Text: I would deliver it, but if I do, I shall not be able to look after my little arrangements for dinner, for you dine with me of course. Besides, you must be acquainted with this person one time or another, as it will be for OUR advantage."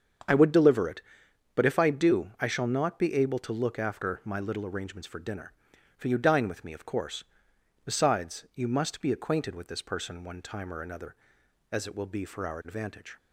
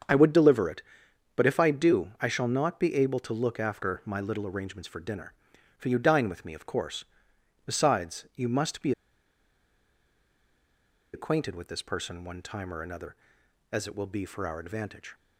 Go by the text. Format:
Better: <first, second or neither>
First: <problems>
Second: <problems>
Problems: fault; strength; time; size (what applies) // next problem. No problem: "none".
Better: first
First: starts louder than the rest; strong; until 1.8 s; 7.5 dB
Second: starts louder than the rest; strong; until 1.6 s; 7.5 dB // pauses between "be" and "acquainted"; strong; at 8.9 s; 2.2 s long